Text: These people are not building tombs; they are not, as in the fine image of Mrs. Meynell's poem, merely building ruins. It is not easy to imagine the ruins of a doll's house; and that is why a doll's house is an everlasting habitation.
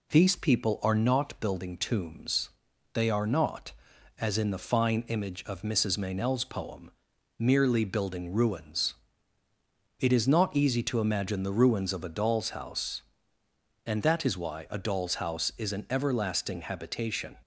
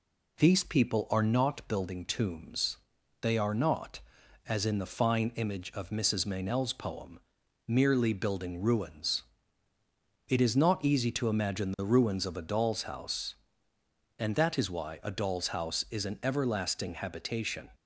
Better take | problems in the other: neither | none

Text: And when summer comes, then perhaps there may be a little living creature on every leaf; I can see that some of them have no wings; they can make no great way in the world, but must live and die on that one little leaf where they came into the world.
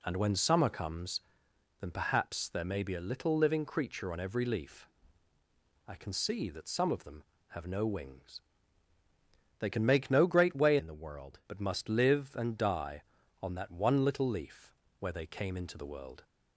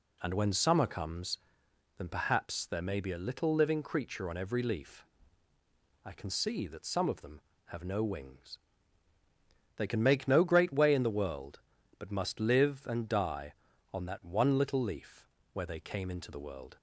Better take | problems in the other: second | changes voice from "in" to "world"; from 10.7 to 11.3 s; 0.6 s long // pauses between "leaf" and "where"; slight; at 14.7 s; 0.28 s long; slight in the second

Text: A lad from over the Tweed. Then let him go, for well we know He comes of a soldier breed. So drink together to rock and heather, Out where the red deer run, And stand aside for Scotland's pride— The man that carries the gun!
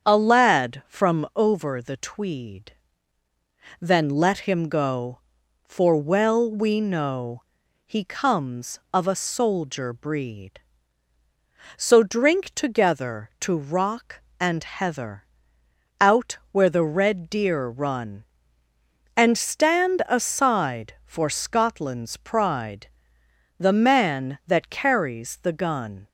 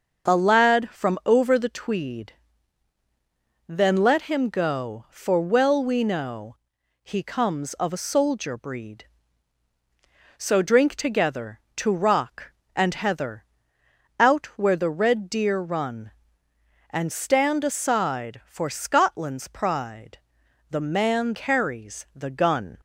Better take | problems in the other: first | starts louder than the rest; until 1.3 s; 6.5 dB; strong in the first // pauses between "know" and "He"; noticeable; at 6.5 s; 0.48 s long; also in the first // skips "that"; at 21.3 s

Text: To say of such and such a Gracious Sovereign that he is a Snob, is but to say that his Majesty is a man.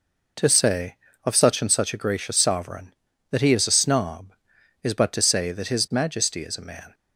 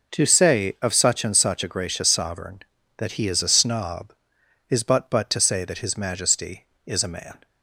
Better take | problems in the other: first | says "but" twice; at 5.0 s

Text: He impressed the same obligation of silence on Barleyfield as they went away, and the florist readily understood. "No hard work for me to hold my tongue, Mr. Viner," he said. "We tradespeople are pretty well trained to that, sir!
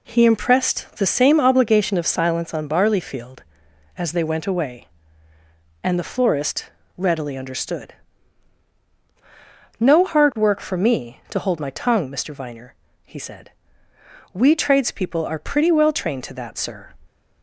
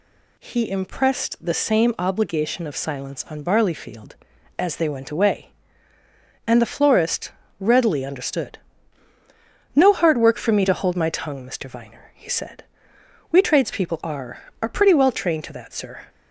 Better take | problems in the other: first | pauses between "florist" and "readily"; slight; at 7.3 s; 0.26 s long; slight in the first // says "are" twice; at 14.6 s

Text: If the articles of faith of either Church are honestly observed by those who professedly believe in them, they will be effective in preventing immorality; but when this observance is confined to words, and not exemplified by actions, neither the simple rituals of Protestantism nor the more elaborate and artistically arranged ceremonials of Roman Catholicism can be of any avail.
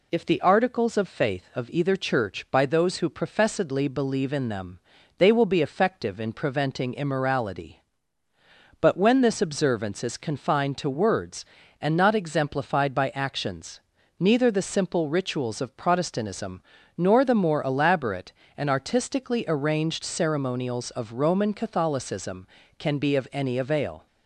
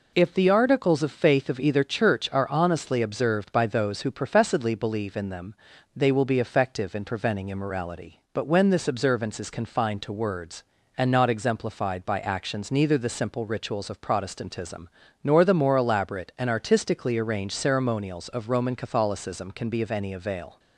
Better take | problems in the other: second | skips "are honestly observed"; at 2.4 s // pauses between "Protestantism" and "nor"; at 16.5 s; 0.38 s long; slight in the second

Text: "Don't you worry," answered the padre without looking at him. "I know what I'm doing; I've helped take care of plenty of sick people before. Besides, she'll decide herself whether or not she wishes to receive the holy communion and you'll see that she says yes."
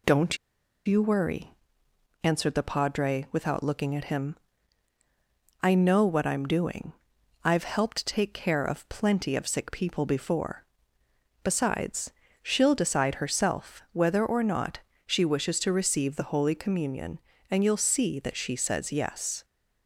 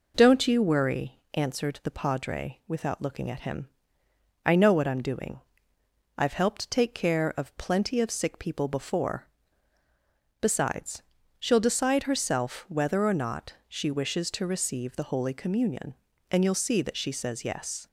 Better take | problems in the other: second | pauses between "Don't" and "you"; noticeable; at 0.3 s; 0.49 s long // pauses between "not" and "she"; slight; at 14.8 s; 0.26 s long

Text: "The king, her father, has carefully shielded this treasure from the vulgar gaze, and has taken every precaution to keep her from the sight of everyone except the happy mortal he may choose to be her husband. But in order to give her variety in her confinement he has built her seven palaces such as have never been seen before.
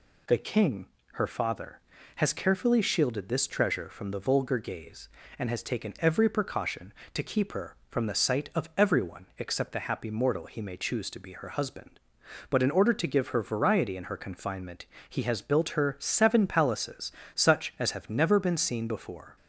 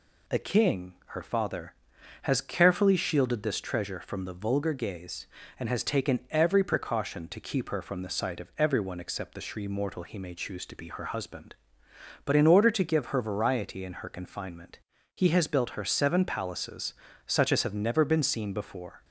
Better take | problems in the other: first | says "shri" for "happy"; at 9.4 s // pauses between "confinement" and "he"; slight; at 14.7 s; 0.36 s long; slight in the first // pauses between "palaces" and "such"; slight; at 16.9 s; 0.32 s long; slight in the first

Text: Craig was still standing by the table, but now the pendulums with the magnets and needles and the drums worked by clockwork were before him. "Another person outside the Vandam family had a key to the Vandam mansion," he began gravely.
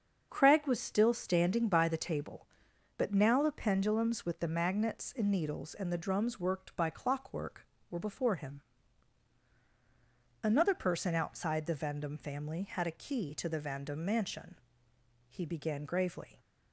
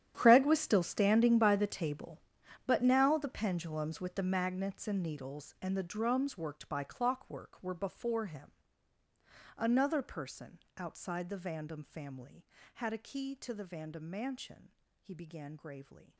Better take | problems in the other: first | gets quieter; strong; throughout; 17 dB // starts louder than the rest; strong; until 1.1 s; 10.5 dB; also in the first // pauses between "person" and "outside"; slight; at 10.5 s; 0.20 s long

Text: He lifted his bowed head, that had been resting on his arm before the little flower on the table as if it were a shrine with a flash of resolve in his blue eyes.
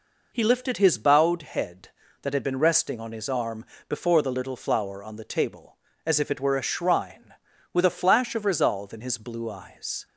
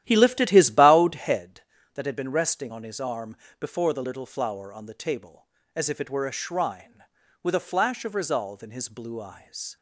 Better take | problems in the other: first | starts louder than the rest; strong; until 1.5 s; 12.5 dB // pauses between "arm" and "before"; slight; at 3.3 s; 0.22 s long; slight in the first

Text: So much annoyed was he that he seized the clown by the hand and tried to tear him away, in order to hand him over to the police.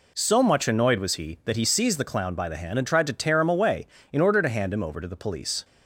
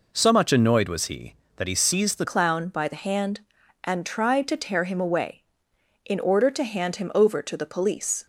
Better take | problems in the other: first | changes voice at "clown"; from 2.2 s on; 6.0 s long

